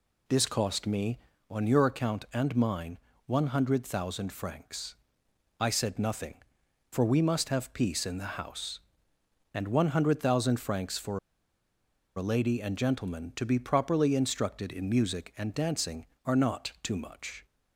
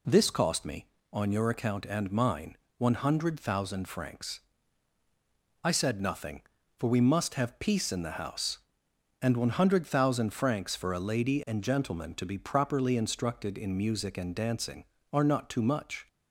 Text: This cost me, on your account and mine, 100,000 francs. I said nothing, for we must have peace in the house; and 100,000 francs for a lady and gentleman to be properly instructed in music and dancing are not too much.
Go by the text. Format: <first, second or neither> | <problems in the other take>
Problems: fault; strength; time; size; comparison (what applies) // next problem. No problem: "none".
second | pauses between "for" and "a"; at 11.1 s; 0.98 s long